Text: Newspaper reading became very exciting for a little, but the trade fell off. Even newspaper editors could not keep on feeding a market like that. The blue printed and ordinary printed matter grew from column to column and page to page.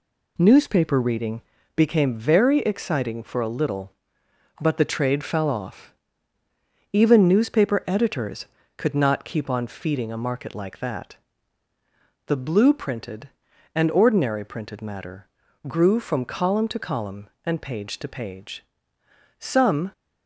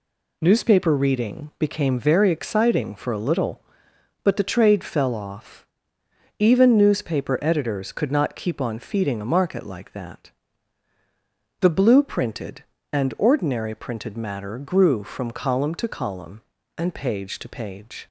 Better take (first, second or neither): second